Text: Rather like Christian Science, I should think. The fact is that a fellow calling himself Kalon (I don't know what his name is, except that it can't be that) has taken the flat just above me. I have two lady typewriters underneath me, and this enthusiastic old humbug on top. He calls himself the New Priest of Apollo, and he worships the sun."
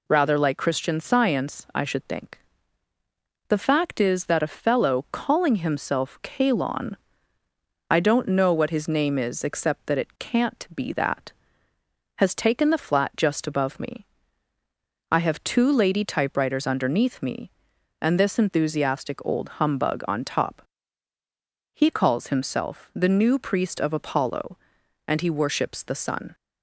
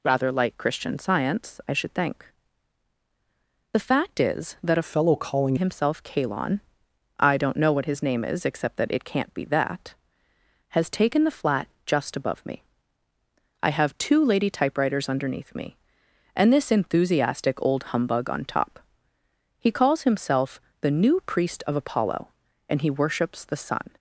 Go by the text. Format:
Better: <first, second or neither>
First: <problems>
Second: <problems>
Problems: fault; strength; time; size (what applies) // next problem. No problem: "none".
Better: first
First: none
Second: changes voice from "fellow" to "calling"; from 4.8 to 5.5 s; 0.7 s long // pauses between "flat" and "just"; slight; at 11.6 s; 0.18 s long // pauses between "himself" and "the"; slight; at 20.5 s; 0.22 s long